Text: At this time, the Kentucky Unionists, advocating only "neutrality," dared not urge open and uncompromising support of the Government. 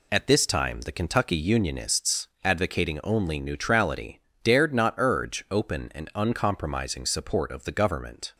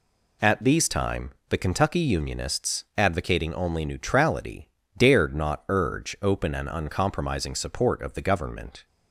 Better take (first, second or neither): first